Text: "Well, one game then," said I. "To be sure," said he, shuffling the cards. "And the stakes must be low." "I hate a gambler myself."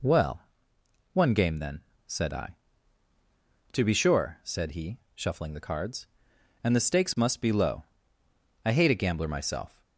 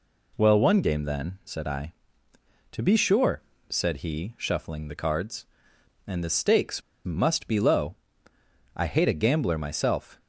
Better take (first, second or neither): first